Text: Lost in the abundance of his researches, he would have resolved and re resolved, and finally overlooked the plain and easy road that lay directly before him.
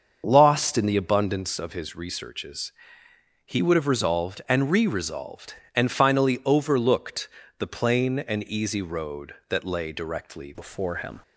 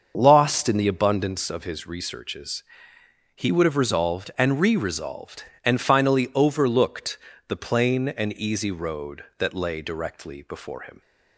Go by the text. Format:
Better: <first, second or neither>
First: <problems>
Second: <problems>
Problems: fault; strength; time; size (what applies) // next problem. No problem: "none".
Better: second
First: starts louder than the rest; until 1.2 s; 6.5 dB // pauses between "overlooked" and "the"; slight; at 7.2 s; 0.30 s long // changes voice at "before"; from 10.5 s on; 0.7 s long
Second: starts louder than the rest; until 1.1 s; 6.5 dB // pauses between "overlooked" and "the"; slight; at 7.1 s; 0.30 s long